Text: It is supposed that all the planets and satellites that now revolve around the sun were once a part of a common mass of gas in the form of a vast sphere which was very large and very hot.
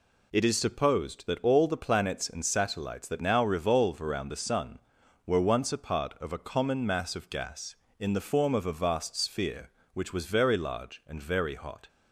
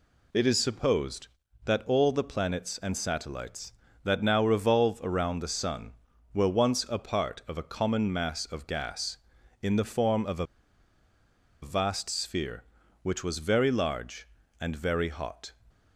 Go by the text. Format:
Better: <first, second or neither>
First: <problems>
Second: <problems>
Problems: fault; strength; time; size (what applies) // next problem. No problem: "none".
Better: first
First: none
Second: pauses between "a" and "vast"; at 10.4 s; 1.1 s long